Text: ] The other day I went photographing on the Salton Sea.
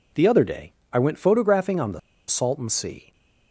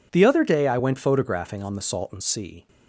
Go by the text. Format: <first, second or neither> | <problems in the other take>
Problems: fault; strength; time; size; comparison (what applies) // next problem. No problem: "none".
second | pauses between "day" and "I"; slight; at 0.7 s; 0.18 s long // pauses between "the" and "Salton"; slight; at 1.9 s; 0.28 s long